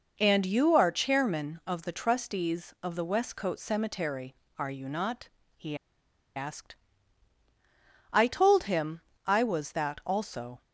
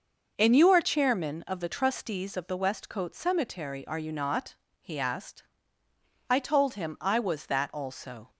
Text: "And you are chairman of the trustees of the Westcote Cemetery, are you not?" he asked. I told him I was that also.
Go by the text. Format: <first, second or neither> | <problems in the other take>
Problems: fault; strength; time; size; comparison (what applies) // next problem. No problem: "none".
second | pauses between "he" and "asked"; noticeable; at 5.7 s; 0.61 s long // pauses between "him" and "I"; slight; at 9.0 s; 0.26 s long